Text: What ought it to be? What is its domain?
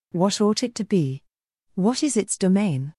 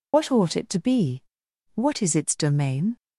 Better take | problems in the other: first | loses the start of "What"; at 0.1 s; 100 ms

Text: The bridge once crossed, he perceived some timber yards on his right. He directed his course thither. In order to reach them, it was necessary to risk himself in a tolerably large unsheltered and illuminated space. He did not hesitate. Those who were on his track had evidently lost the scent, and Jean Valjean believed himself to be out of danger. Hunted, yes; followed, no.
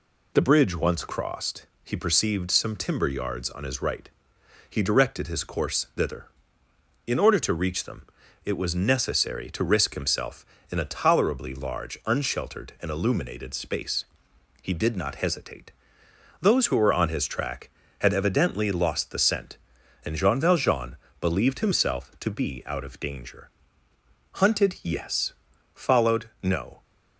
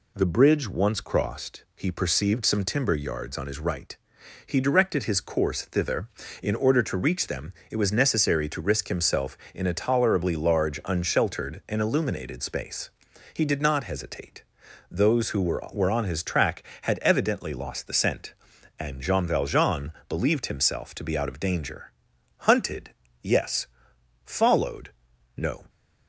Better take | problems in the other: first | says "were" twice; at 15.7 s // pauses between "Valjean" and "believed"; slight; at 19.9 s; 0.18 s long; slight in the first

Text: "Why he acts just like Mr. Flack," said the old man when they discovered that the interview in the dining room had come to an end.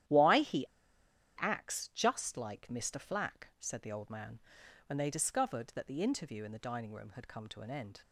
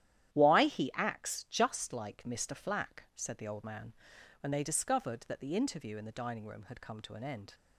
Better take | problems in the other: second | starts louder than the rest; strong; until 1.7 s; 11.5 dB; strong in the second // pauses between "he" and "acts"; noticeable; at 0.6 s; 0.70 s long // pauses between "man" and "when"; noticeable; at 4.4 s; 0.46 s long; noticeable in the second

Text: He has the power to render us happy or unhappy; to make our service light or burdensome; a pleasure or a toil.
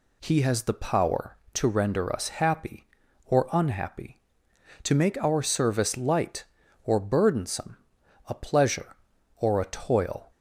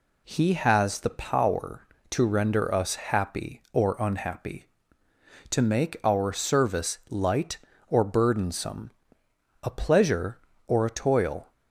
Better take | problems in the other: neither | none

